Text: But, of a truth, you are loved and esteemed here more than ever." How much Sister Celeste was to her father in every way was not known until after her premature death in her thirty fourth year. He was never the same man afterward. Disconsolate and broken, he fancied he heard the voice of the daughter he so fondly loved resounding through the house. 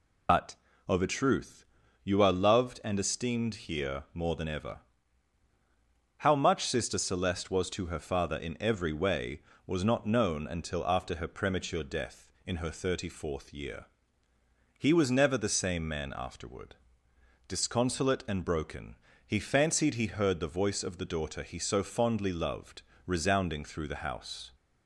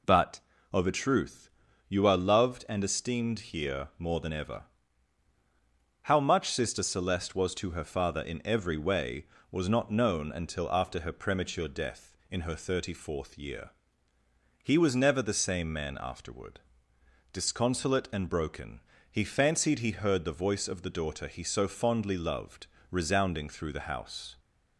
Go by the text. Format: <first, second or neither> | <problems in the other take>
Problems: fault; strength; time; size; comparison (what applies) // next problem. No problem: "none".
second | loses the start of "But"; at 0.2 s; 90 ms // pauses between "loved" and "resounding"; slight; at 22.8 s; 0.24 s long; slight in the second